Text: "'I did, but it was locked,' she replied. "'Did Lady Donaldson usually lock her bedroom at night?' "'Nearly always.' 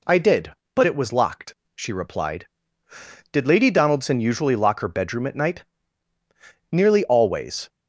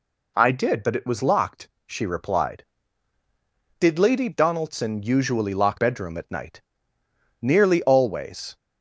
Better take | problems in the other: first | skips "her"; at 5.7 s

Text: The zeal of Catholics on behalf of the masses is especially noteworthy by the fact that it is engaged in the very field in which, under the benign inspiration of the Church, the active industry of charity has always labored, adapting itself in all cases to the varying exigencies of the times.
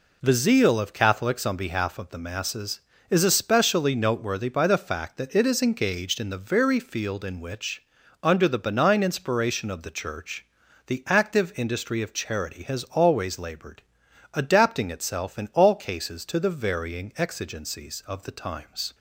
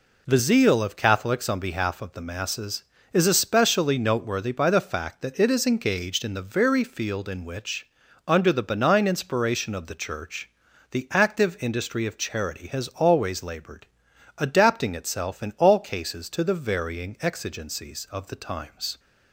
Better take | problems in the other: neither | none

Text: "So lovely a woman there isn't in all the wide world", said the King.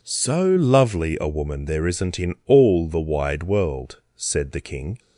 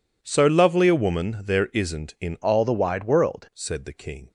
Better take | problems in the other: first | changes voice from "all" to "world"; from 2.4 to 3.4 s; 1.0 s long

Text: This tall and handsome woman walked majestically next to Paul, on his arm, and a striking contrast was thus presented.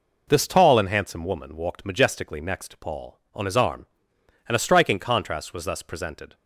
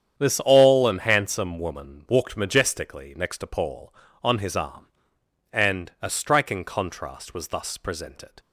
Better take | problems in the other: first | starts louder than the rest; strong; until 1.2 s; 8.5 dB // says "all" for "tall"; at 0.4 s

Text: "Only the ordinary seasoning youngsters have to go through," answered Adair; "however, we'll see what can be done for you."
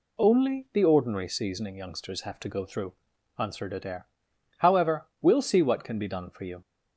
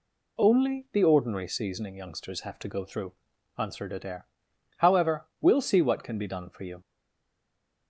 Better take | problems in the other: first | stays silent after the last word; from 6.8 s on; 1.0 s long

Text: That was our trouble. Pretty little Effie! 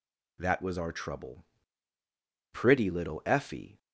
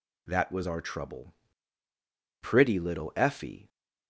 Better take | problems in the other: neither | none

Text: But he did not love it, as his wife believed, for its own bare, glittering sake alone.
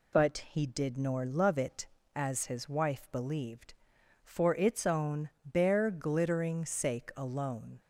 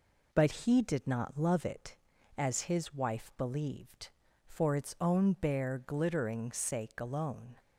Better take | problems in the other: second | says "nor" for "not"; at 0.9 s

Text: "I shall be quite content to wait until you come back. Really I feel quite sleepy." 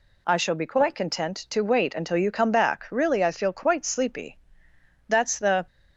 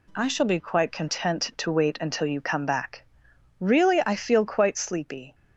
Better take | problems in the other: second | goes on to say "That's the"; from 5.0 s on; 0.60 s long

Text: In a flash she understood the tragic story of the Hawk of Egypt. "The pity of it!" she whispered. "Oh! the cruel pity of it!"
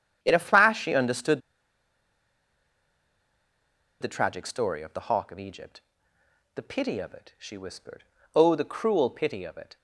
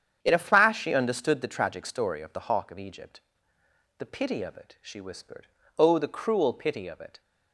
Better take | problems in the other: second | starts louder than the rest; strong; until 1.2 s; 8.5 dB; strong in the second // pauses between "understood" and "the"; strong; at 1.4 s; 2.5 s long

